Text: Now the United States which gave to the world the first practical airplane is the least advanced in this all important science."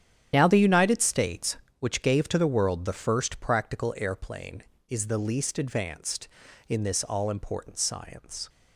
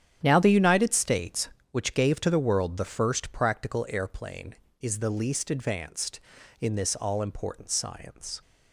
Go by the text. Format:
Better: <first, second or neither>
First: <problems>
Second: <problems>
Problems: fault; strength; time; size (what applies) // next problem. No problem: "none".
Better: second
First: loses the start of "Now"; at 0.3 s; 25 ms // starts louder than the rest; strong; until 1.3 s; 10 dB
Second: starts louder than the rest; strong; until 1.2 s; 9.5 dB